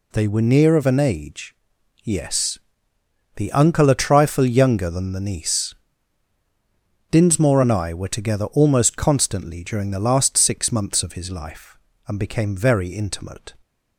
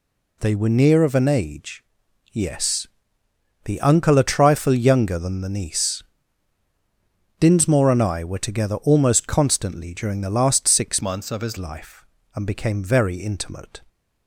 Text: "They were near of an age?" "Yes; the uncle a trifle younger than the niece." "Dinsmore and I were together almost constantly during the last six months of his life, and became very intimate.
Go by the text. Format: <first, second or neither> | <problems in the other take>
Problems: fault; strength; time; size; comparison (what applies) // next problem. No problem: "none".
first | changes voice from "months" to "his"; from 11.0 to 11.5 s; 0.5 s long